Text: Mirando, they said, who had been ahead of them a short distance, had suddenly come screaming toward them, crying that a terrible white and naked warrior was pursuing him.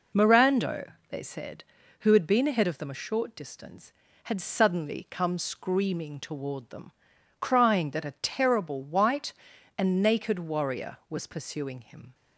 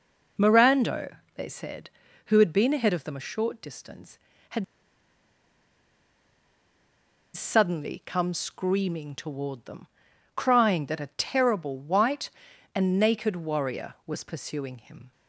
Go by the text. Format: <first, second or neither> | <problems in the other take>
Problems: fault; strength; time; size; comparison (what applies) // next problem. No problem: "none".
first | pauses between "had" and "suddenly"; strong; at 4.6 s; 2.7 s long